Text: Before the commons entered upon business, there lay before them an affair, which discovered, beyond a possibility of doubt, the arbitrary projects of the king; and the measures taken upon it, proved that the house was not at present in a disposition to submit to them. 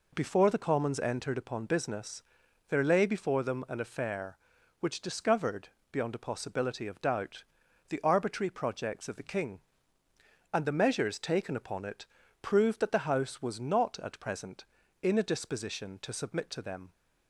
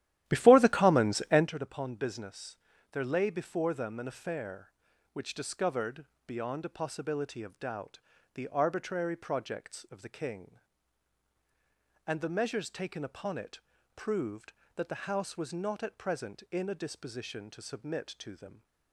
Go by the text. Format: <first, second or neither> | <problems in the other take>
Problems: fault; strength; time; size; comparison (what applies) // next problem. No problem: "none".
first | starts louder than the rest; strong; until 1.5 s; 13 dB